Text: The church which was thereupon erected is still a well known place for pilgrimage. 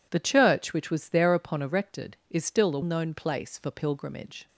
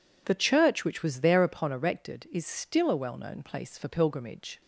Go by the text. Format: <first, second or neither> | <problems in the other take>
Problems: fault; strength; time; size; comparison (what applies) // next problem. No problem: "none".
second | skips "well"; at 2.8 s